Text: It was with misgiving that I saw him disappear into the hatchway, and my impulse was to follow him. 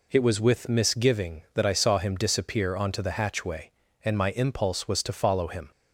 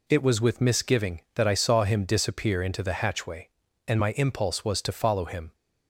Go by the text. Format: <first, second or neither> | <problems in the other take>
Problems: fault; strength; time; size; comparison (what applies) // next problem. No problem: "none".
second | says "onto" for "into"; at 2.7 s